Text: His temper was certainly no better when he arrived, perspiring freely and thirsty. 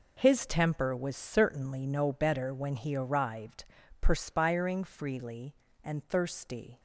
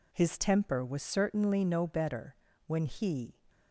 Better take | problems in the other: first | pauses between "better" and "when"; slight; at 2.3 s; 0.32 s long // stops before "arrived perspiring freely and thirsty"; at 3.4 s

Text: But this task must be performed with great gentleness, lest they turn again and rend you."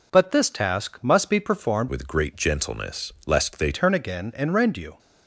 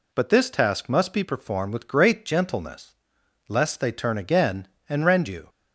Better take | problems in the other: second | changes voice from "with" to "they"; from 1.8 to 3.7 s; 1.9 s long

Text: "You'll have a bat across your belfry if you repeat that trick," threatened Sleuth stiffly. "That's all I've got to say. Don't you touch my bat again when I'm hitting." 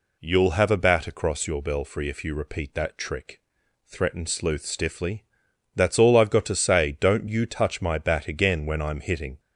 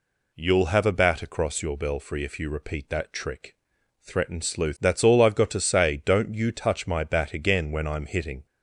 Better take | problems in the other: first | skips "stiffly"; at 4.7 s

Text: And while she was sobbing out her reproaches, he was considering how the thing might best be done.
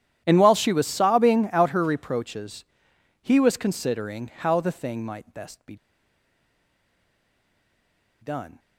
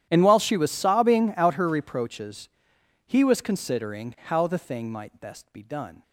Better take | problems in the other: second | starts louder than the rest; strong; until 1.2 s; 11 dB; strong in the second // pauses between "be" and "done"; strong; at 5.7 s; 2.4 s long

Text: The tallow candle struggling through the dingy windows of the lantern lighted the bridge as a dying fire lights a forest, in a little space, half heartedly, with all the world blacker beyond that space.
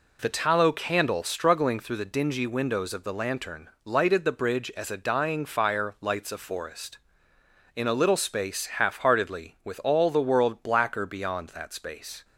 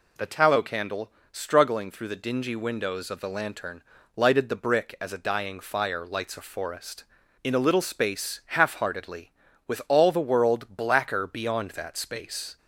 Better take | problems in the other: first | pauses between "candle" and "struggling"; slight; at 1.1 s; 0.20 s long // pauses between "lantern" and "lighted"; slight; at 3.8 s; 0.32 s long; slight in the first // says "brick" for "bridge"; at 4.5 s

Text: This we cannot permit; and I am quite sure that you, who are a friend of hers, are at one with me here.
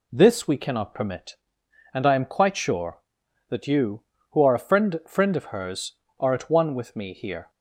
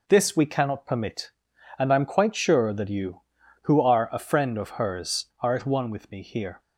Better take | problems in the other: second | says "friend" twice; at 5.0 s

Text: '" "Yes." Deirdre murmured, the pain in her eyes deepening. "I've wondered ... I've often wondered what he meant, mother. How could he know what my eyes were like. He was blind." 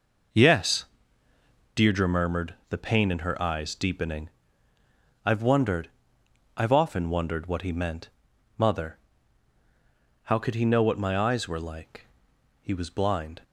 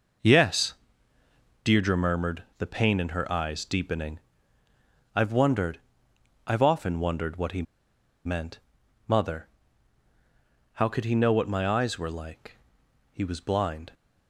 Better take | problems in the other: first | pauses between "he" and "meant"; noticeable; at 7.6 s; 0.62 s long

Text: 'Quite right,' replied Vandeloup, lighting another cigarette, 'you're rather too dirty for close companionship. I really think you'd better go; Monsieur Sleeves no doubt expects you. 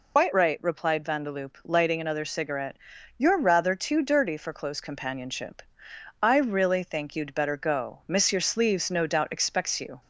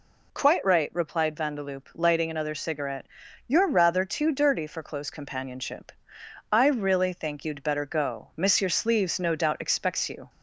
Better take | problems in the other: second | loses the start of "Quite"; at 0.1 s; 140 ms

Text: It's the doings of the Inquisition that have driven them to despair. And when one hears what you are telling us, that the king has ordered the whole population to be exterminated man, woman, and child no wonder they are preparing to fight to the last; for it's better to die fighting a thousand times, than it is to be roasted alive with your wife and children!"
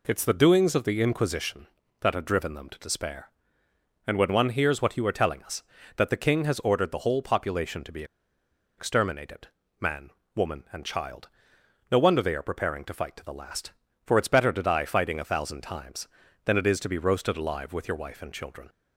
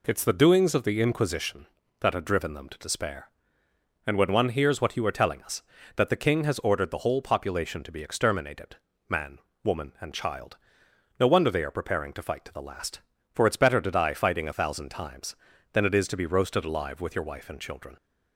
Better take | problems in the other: second | pauses between "be" and "exterminated"; noticeable; at 8.0 s; 0.74 s long // pauses between "exterminated" and "man"; slight; at 9.4 s; 0.34 s long; slight in the second // pauses between "child" and "no"; noticeable; at 11.2 s; 0.62 s long; noticeable in the second

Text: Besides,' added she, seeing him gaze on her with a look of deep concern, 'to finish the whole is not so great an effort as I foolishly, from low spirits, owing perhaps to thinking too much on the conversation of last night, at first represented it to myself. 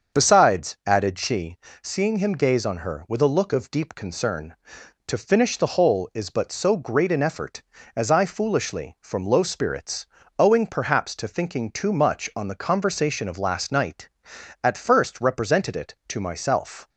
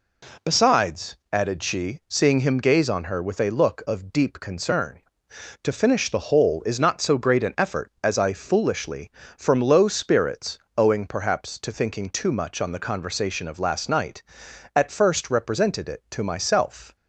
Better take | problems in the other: second | starts louder than the rest; until 1.2 s; 6.5 dB // says "but" for "not"; at 6.3 s

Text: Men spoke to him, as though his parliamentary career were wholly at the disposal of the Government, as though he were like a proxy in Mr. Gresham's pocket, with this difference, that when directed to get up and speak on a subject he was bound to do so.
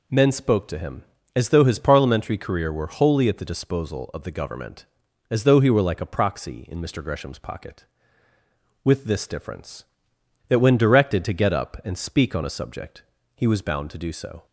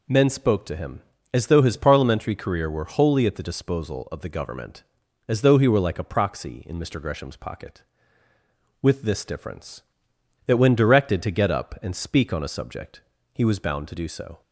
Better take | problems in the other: neither | pauses between "subject" and "he"; slight; the same in both

